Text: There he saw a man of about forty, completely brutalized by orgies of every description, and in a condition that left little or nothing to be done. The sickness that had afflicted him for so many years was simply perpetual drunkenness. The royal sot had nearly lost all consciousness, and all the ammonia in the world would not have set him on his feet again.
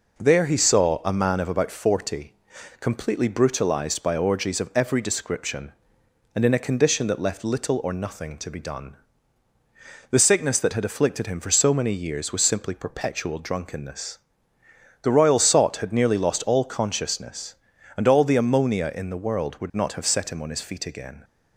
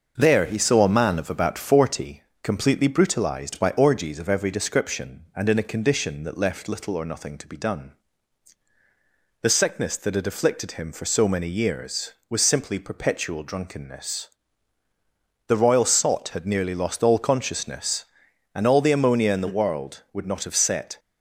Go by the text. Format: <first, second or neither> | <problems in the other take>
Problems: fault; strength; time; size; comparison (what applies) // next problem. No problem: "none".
first | starts louder than the rest; until 1.1 s; 6 dB // stops before "him on his feet again"; at 20.9 s